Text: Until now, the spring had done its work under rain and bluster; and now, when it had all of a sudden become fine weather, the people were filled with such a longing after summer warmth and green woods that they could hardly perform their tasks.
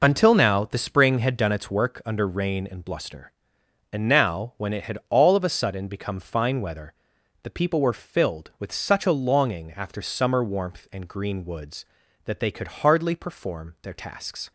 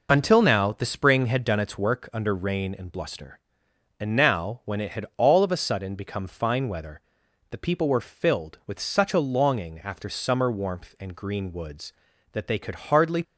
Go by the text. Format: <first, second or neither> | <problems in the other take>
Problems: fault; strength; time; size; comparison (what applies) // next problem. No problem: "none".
first | stops before "perform their tasks"; at 13.2 s